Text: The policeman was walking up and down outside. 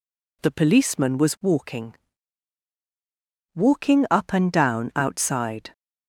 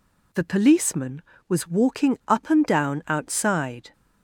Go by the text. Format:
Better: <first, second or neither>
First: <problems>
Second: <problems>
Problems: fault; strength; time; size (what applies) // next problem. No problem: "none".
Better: second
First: says "walking" twice; at 3.5 s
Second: none